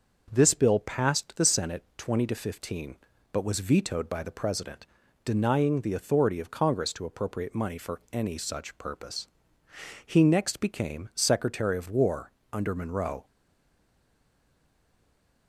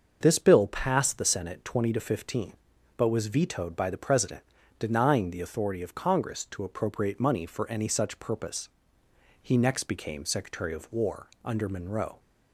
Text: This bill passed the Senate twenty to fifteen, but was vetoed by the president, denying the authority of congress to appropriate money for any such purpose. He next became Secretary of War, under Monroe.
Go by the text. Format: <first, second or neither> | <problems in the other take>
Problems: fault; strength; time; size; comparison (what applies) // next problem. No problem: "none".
second | starts louder than the rest; until 1.3 s; 6.5 dB; also in the second // stays silent after the last word; from 13.2 s on; 2.2 s long